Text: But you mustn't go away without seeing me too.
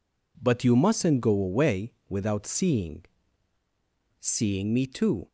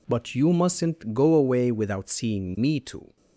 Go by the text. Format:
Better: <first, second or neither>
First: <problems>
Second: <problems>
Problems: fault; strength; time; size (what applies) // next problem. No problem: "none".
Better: second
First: pauses between "away" and "without"; slight; at 1.9 s; 0.16 s long // says "seeing" twice; at 4.1 s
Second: none